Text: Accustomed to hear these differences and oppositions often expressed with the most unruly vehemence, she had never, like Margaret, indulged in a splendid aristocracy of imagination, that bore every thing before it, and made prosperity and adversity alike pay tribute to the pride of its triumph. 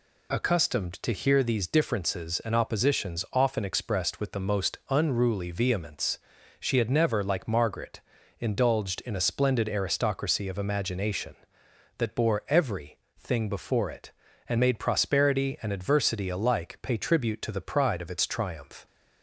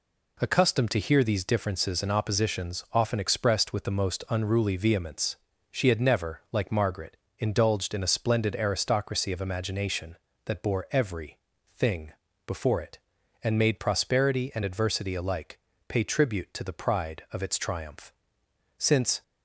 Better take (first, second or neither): first